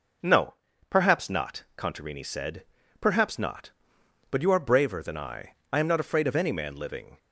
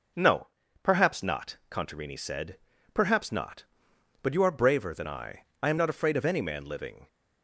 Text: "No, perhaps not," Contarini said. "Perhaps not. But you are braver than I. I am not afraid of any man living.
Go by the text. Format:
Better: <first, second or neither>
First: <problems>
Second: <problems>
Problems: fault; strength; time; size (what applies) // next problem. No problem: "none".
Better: neither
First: none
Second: none